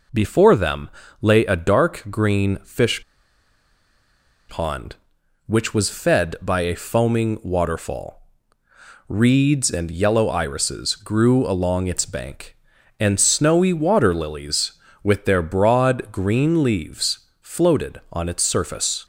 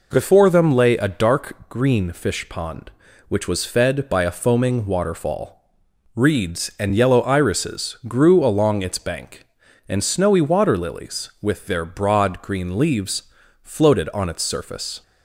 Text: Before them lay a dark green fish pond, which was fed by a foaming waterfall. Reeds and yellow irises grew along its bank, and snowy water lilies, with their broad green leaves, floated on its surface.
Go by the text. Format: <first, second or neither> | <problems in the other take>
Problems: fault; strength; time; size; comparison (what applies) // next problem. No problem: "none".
second | pauses between "them" and "lay"; slight; at 0.8 s; 0.32 s long // pauses between "fish" and "pond"; strong; at 3.0 s; 1.4 s long